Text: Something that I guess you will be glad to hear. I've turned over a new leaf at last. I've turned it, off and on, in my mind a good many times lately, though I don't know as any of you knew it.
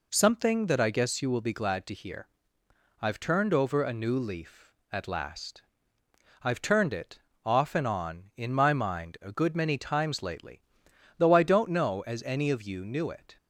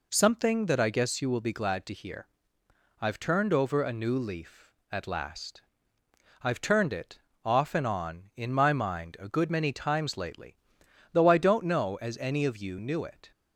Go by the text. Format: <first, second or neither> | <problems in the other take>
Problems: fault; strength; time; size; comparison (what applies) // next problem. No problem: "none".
neither | none